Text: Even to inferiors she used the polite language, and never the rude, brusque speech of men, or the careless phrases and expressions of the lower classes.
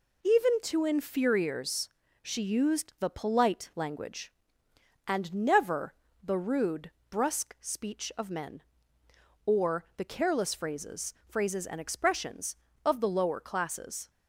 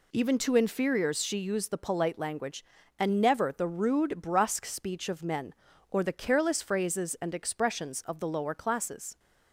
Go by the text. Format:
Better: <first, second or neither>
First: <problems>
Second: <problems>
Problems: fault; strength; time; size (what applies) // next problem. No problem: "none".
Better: second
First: pauses between "inferiors" and "she"; slight; at 1.8 s; 0.32 s long // pauses between "never" and "the"; slight; at 5.9 s; 0.28 s long // says "phrases" twice; at 11.2 s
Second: none